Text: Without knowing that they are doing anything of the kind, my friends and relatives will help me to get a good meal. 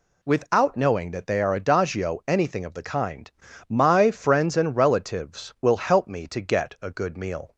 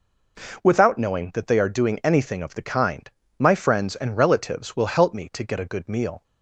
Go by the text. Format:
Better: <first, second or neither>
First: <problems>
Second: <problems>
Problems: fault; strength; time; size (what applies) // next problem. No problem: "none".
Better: second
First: says "adagio" for "doing"; at 1.5 s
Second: none